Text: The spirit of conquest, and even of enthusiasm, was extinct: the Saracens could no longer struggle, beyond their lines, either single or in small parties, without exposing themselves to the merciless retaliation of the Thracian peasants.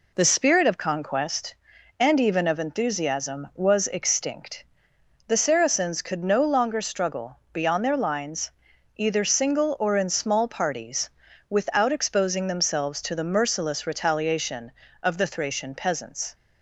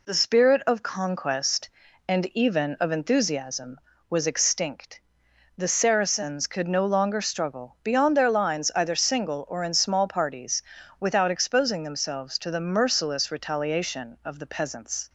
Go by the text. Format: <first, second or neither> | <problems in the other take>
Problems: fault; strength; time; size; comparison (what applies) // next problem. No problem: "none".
first | skips "Thracian"; at 14.4 s